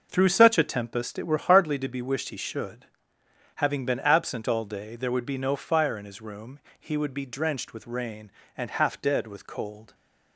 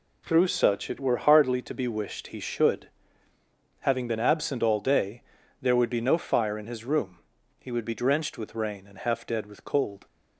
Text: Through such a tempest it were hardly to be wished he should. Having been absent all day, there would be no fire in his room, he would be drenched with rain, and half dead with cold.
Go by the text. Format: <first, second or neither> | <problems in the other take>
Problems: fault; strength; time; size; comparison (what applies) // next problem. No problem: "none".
first | skips "a tempest"; at 0.8 s